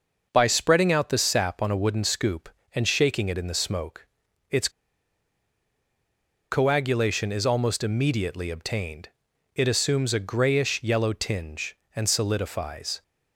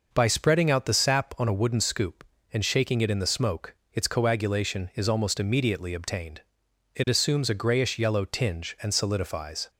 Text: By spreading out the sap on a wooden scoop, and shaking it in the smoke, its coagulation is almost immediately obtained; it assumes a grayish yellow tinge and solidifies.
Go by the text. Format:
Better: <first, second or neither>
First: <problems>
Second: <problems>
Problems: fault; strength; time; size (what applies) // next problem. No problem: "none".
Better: second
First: pauses between "its" and "coagulation"; strong; at 4.6 s; 1.8 s long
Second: none